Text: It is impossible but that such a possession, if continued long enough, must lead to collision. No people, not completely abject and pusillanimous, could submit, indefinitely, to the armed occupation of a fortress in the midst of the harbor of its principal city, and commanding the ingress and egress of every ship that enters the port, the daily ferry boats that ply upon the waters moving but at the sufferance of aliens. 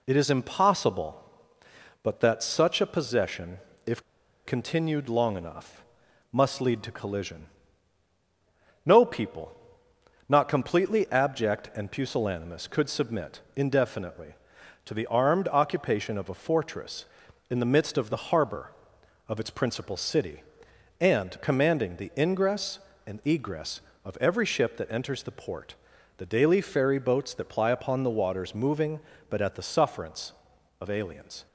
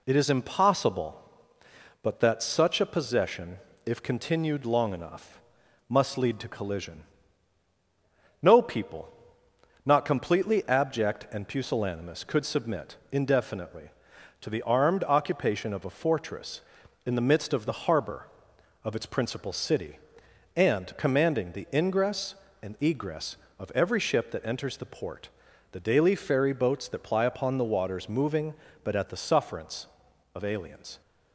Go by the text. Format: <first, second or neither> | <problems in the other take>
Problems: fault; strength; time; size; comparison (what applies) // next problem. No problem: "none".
second | pauses between "if" and "continued"; at 4.0 s; 0.44 s long